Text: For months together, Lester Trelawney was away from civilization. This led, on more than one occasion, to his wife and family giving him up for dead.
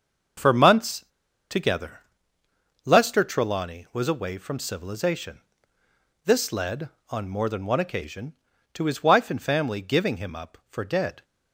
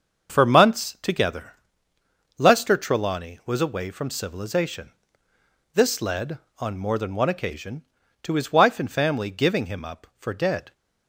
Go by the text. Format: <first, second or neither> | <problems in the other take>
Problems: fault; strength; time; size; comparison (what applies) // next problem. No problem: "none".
second | starts louder than the rest; until 1.8 s; 6.5 dB; also in the second // pauses between "months" and "together"; noticeable; at 1.0 s; 0.46 s long